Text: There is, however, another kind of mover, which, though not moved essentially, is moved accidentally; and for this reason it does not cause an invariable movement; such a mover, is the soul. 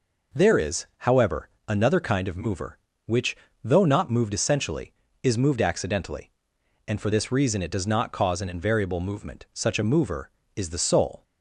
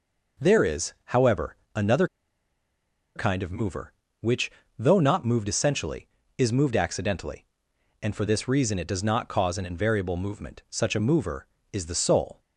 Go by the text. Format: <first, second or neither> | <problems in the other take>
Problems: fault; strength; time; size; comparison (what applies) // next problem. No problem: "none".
first | pauses between "another" and "kind"; at 2.0 s; 1.0 s long